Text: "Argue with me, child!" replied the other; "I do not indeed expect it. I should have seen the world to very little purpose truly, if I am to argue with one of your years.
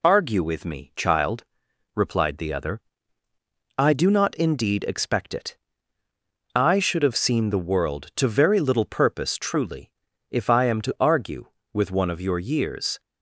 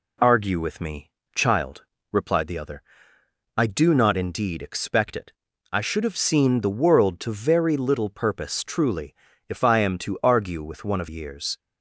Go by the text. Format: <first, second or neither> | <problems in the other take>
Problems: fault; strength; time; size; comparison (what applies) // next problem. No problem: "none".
first | skips "your"; at 11.0 s